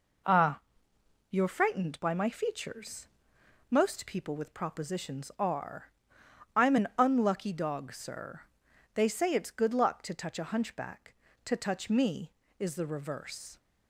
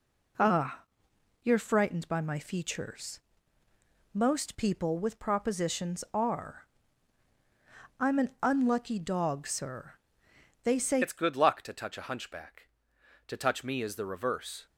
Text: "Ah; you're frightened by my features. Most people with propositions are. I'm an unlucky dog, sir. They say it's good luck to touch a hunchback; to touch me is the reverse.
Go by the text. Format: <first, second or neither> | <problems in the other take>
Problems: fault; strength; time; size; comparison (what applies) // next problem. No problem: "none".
first | changes voice at "it's"; from 11.0 s on; 3.6 s long